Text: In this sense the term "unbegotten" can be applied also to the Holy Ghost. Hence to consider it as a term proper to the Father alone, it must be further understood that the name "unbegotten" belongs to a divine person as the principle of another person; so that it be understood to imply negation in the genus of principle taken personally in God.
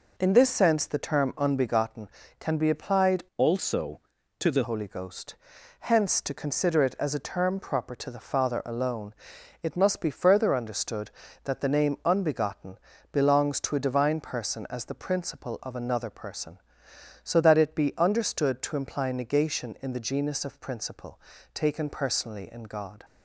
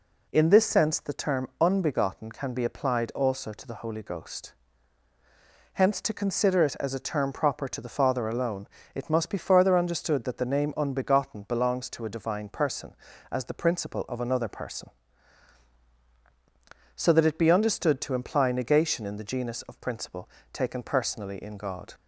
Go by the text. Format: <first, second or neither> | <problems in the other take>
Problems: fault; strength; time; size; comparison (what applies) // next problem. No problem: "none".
second | changes voice from "also" to "the"; from 3.3 to 4.6 s; 1.3 s long // pauses between "unbegotten" and "belongs"; slight; at 12.7 s; 0.34 s long // pauses between "principle" and "taken"; slight; at 21.1 s; 0.34 s long; slight in the second